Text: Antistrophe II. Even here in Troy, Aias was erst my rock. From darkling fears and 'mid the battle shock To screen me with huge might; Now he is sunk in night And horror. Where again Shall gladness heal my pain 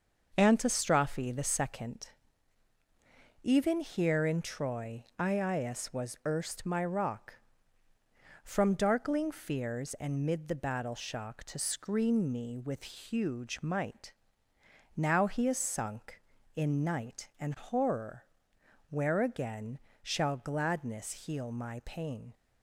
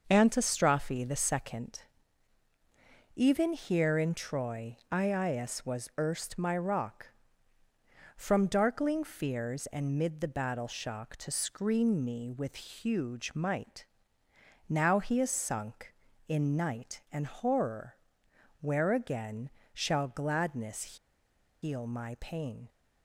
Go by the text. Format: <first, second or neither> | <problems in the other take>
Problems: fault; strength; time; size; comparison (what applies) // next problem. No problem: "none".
first | starts louder than the rest; noticeable; until 1.1 s; 6 dB; noticeable in the first // pauses between "again" and "Shall"; slight; at 19.4 s; 0.24 s long; slight in the first // pauses between "gladness" and "heal"; noticeable; at 20.9 s; 0.64 s long